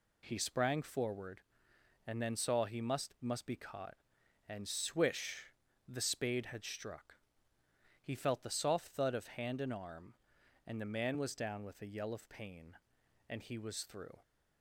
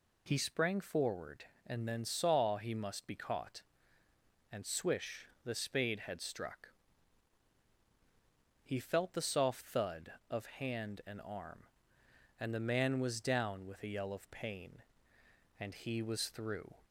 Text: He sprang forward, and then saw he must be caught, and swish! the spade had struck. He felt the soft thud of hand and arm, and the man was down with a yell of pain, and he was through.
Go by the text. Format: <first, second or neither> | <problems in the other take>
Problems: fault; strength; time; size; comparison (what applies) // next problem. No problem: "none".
second | says "must" twice; at 3.1 s